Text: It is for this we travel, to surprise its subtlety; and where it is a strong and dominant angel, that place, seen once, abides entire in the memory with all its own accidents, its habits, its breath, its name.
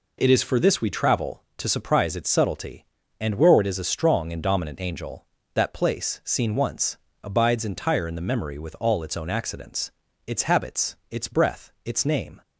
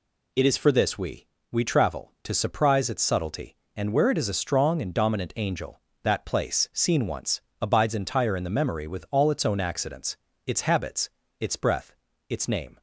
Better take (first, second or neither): first